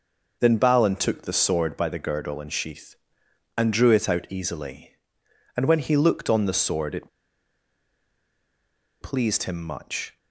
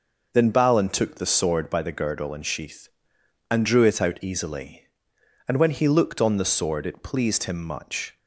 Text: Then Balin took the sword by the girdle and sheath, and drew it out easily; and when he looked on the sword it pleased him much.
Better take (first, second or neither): second